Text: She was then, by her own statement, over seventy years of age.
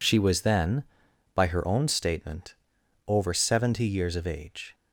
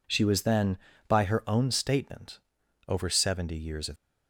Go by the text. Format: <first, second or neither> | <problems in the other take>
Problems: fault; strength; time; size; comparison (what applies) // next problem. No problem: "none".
first | stops before "age"; at 3.9 s